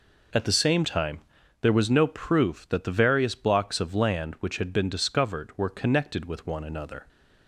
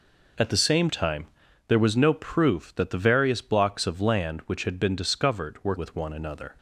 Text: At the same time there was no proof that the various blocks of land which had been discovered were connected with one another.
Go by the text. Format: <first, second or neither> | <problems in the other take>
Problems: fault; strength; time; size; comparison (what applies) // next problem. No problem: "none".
first | pauses between "time" and "there"; at 1.2 s; 0.40 s long; also in the first // skips "connected"; at 5.7 s